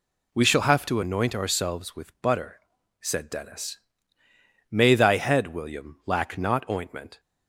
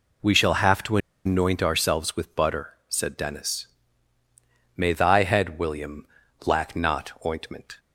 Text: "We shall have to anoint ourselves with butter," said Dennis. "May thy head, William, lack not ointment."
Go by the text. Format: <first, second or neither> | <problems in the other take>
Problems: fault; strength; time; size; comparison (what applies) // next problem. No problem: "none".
first | pauses between "to" and "anoint"; slight; at 0.9 s; 0.27 s long